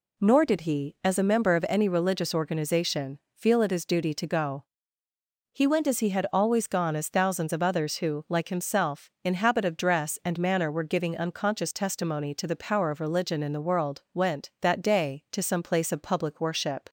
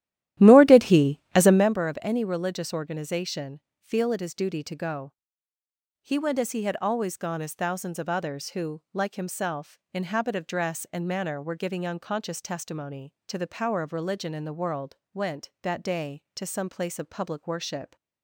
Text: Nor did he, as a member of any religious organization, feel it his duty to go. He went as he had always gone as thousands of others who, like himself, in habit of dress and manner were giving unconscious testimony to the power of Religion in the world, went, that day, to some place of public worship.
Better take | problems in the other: first | starts louder than the rest; strong; until 1.8 s; 13.5 dB

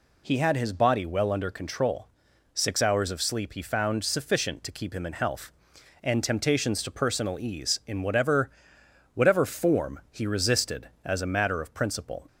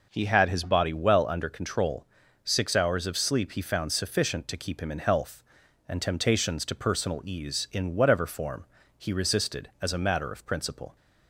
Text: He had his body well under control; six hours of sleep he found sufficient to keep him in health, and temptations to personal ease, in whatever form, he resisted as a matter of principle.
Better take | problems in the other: second | says "whatever" twice; at 9.1 s

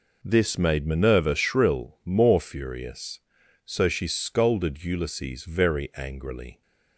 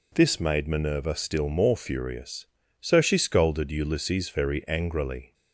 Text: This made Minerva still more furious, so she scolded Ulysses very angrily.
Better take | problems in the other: second | says "shrill" for "still"; at 1.3 s

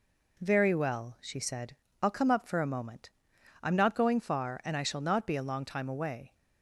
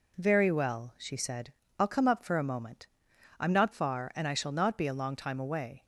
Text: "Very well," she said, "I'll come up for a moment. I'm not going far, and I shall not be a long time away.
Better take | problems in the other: first | skips "going"; at 3.7 s

